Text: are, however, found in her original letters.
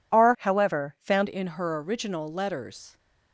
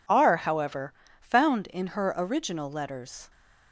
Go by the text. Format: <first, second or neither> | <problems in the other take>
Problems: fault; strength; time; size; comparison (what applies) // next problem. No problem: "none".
second | changes voice from "however" to "found"; from 0.3 to 1.2 s; 0.9 s long